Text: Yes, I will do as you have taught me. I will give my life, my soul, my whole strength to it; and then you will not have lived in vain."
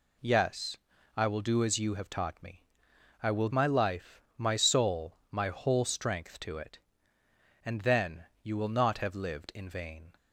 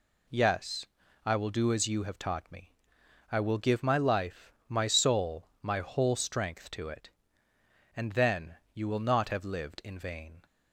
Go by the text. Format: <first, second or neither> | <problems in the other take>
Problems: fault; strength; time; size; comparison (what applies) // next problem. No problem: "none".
second | skips "give"; at 3.4 s // pauses between "then" and "you"; slight; at 8.2 s; 0.18 s long; slight in the second